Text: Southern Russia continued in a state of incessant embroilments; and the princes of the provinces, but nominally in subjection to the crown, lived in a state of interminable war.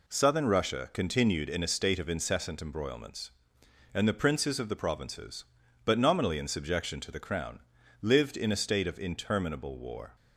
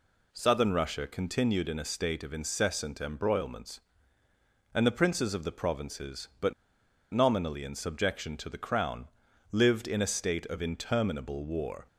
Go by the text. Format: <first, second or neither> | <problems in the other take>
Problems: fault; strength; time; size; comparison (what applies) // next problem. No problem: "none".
first | pauses between "but" and "nominally"; noticeable; at 6.5 s; 0.59 s long